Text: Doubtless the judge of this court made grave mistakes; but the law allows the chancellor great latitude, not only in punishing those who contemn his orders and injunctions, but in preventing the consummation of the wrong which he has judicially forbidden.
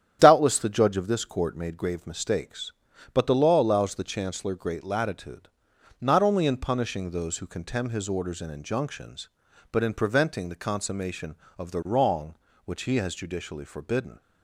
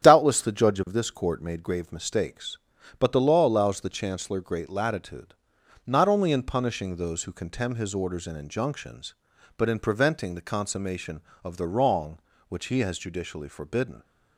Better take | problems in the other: neither | starts louder than the rest; strong; the same in both

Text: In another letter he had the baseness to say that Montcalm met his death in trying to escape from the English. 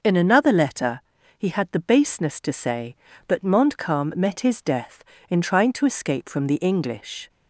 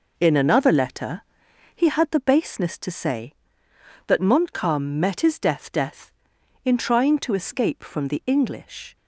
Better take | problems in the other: first | pauses between "letter" and "he"; noticeable; at 1.2 s; 0.54 s long; also in the first // says "death" twice; at 5.7 s

